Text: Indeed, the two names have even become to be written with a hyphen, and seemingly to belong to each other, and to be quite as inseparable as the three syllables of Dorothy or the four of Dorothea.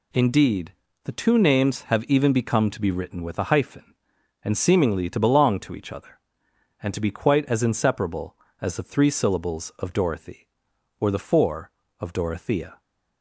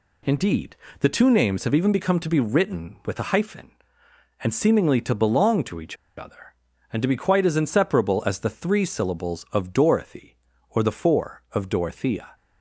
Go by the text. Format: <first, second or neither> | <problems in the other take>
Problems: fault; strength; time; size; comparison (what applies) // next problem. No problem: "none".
first | pauses between "each" and "other"; slight; at 5.9 s; 0.21 s long